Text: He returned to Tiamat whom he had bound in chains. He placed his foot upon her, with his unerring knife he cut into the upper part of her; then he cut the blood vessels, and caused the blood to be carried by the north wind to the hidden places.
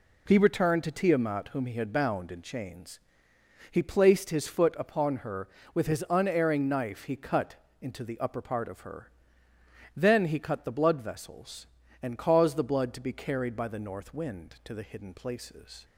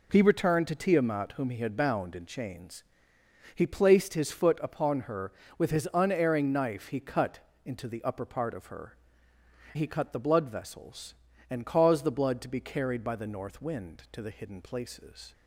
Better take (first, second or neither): first